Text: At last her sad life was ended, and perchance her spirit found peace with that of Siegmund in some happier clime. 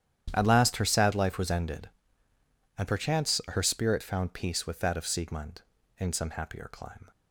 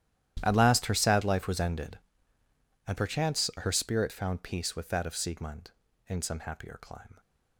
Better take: first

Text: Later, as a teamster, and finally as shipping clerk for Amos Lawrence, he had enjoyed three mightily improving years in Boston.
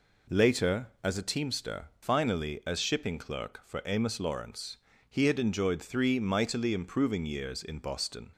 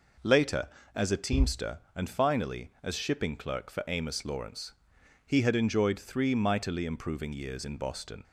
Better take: second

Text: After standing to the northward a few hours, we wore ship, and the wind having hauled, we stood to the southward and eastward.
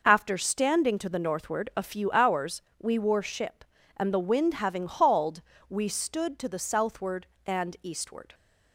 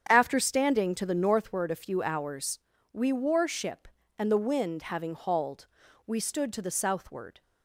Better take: first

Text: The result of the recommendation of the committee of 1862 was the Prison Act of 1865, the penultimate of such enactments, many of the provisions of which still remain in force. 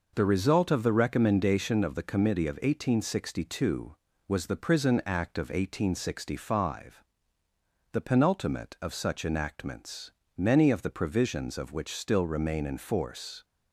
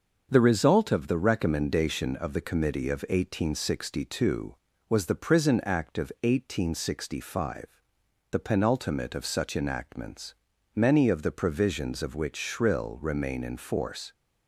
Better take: first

